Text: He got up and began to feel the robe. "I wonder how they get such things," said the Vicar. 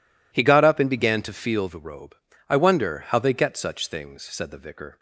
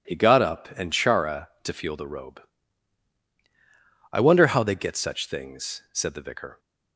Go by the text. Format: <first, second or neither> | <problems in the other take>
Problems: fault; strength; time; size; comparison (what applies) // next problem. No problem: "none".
first | says "chara" for "began"; at 0.9 s